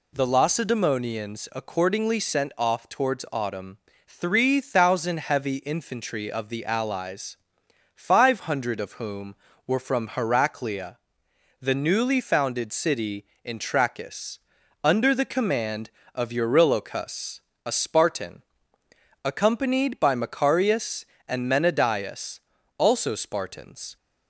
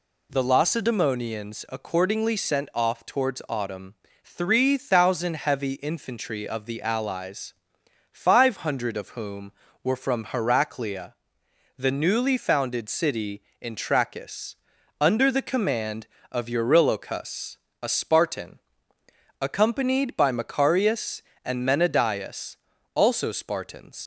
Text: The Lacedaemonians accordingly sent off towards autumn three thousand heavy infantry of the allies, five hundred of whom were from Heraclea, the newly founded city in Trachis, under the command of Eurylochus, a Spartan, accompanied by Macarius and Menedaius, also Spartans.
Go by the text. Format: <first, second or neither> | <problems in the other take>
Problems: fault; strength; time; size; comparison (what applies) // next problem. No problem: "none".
first | pauses between "autumn" and "three"; slight; at 3.9 s; 0.28 s long; slight in the first // leaves "Spartans" unfinished; at 24.0 s; 70 ms